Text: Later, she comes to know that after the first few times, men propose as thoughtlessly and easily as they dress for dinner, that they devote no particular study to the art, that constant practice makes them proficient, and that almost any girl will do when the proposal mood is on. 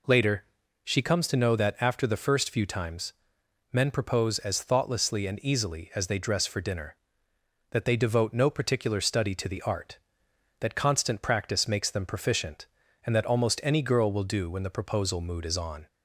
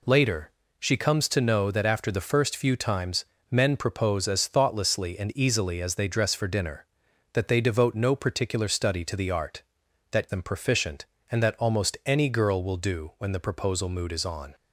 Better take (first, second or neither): first